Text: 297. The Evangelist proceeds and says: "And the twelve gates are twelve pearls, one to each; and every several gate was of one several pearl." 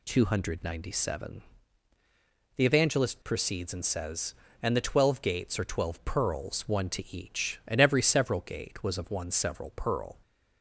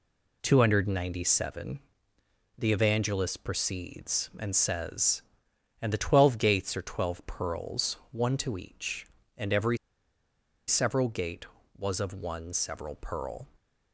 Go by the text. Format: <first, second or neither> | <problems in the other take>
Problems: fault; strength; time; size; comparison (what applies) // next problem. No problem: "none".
first | pauses between "every" and "several"; noticeable; at 9.7 s; 0.92 s long